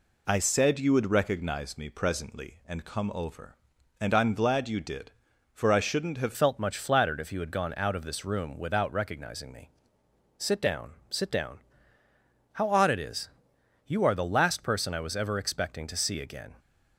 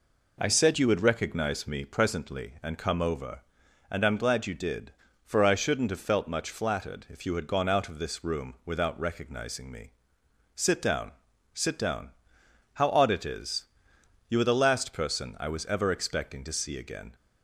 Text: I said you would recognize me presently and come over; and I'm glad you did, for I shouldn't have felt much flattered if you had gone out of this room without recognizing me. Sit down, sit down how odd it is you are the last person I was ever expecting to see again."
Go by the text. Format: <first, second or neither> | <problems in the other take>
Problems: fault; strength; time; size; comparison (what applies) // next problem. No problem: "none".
second | changes voice at "felt"; from 6.3 s on; 10.2 s long // pauses between "down" and "how"; noticeable; at 11.5 s; 0.94 s long; noticeable in the second // pauses between "is" and "you"; noticeable; at 13.2 s; 0.56 s long; noticeable in the second